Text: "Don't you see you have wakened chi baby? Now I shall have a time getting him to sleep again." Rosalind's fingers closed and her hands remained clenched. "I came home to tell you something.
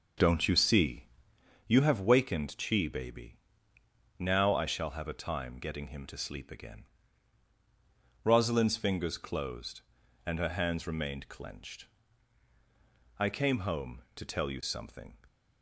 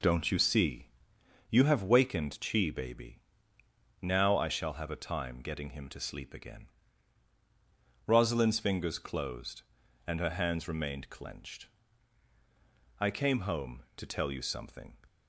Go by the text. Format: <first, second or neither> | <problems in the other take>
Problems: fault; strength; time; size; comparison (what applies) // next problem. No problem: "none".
second | starts louder than the rest; until 1.3 s; 6 dB // pauses between "see" and "you"; noticeable; at 1.0 s; 0.64 s long; noticeable in the second